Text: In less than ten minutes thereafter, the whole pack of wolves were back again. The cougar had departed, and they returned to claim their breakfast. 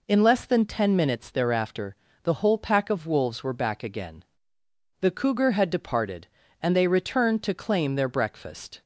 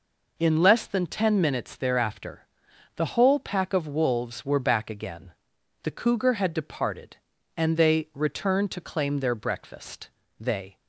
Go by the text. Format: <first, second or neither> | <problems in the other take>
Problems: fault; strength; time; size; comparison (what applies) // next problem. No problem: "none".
first | goes on to say "They"; slight; from 10.3 s on; 0.38 s long